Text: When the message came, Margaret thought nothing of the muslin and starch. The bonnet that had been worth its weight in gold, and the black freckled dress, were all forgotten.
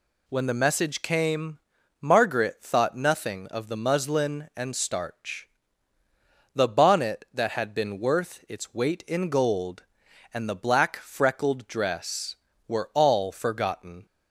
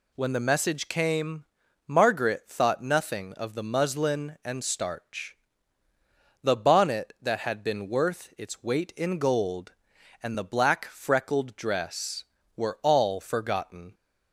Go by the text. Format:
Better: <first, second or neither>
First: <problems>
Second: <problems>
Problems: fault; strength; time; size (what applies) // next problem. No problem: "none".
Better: neither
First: none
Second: none